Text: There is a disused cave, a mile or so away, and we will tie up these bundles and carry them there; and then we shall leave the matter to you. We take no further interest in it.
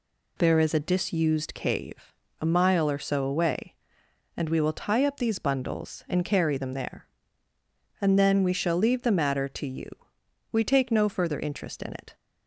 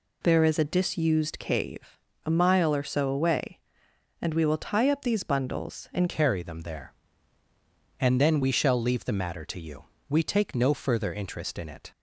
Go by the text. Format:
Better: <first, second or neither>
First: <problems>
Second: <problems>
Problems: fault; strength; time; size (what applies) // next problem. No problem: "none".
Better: first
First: none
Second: changes voice at "carry"; from 6.0 s on; 5.9 s long